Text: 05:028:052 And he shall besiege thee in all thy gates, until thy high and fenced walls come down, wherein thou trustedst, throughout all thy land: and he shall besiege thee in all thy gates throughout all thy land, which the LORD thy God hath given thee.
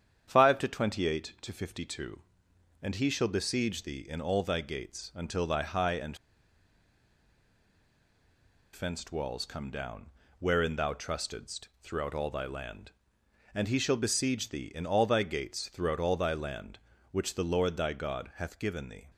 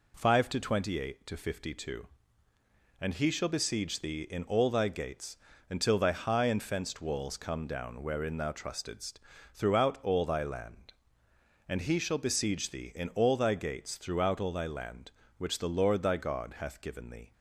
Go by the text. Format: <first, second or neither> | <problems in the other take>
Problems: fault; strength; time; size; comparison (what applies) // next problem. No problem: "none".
second | starts louder than the rest; strong; until 1.2 s; 8.5 dB // pauses between "and" and "fenced"; strong; at 6.1 s; 2.5 s long